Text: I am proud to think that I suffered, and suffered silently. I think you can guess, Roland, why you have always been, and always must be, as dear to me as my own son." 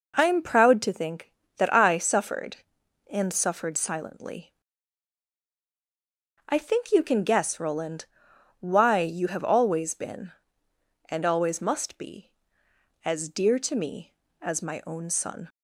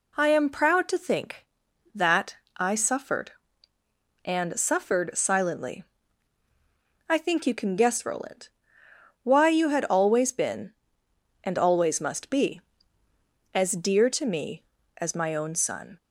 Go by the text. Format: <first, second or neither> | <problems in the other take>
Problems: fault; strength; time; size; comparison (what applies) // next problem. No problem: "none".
first | pauses between "that" and "I"; slight; at 2.3 s; 0.22 s long // says "had" for "have"; at 9.6 s